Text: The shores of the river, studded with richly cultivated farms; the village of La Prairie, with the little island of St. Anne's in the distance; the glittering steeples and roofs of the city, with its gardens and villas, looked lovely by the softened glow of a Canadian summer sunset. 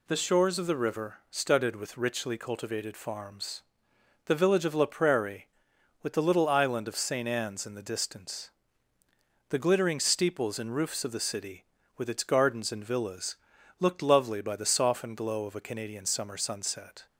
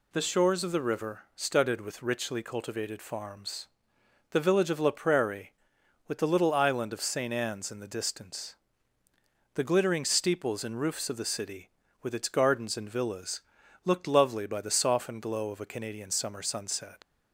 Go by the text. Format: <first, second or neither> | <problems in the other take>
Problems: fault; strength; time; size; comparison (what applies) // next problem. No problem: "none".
first | leaves "sunset" unfinished; at 17.0 s; 90 ms